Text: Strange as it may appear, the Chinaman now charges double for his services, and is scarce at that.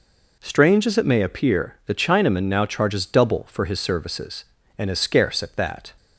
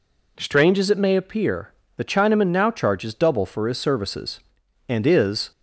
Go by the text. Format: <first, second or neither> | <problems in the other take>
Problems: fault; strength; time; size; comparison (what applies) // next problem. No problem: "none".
first | stops before "scarce at that"; at 5.5 s